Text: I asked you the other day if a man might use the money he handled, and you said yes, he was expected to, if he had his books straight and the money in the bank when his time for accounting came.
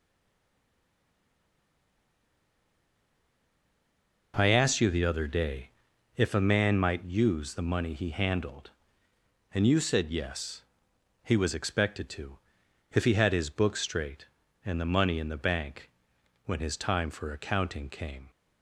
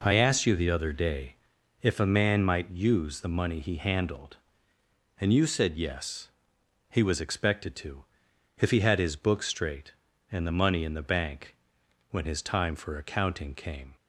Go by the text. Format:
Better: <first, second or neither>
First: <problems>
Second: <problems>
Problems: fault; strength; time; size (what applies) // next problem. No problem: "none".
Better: second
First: stays silent before the first word; strong; until 4.3 s; 4.3 s long // pauses between "day" and "if"; noticeable; at 5.6 s; 0.48 s long // pauses between "bank" and "when"; noticeable; at 15.8 s; 0.58 s long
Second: pauses between "day" and "if"; noticeable; at 1.3 s; 0.48 s long // pauses between "bank" and "when"; noticeable; at 11.5 s; 0.58 s long